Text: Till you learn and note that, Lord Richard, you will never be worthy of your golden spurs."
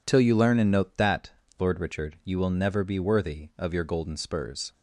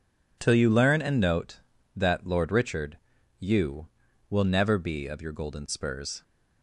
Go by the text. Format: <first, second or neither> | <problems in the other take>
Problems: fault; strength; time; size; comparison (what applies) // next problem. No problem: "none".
first | skips "worthy"; at 5.0 s